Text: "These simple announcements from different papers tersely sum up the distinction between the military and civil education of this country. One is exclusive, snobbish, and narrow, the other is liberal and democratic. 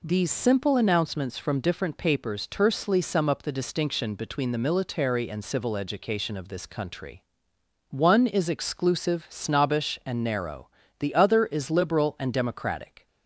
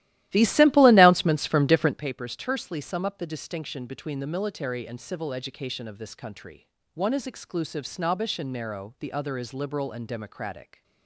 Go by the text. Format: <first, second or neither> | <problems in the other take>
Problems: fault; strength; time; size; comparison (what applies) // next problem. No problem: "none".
first | starts louder than the rest; strong; until 2.0 s; 15 dB